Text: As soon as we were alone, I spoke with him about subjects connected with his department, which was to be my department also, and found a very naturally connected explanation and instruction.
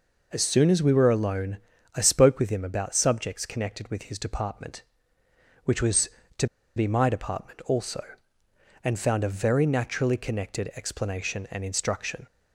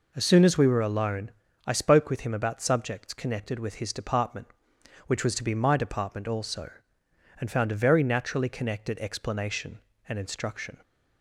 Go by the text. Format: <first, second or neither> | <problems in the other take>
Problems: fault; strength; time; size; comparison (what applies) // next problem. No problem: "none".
second | pauses between "to" and "be"; slight; at 6.4 s; 0.30 s long